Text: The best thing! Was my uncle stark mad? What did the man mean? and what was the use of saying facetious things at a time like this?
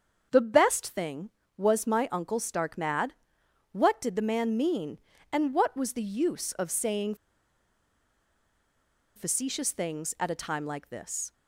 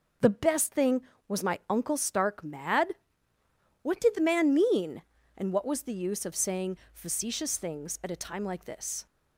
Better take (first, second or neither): second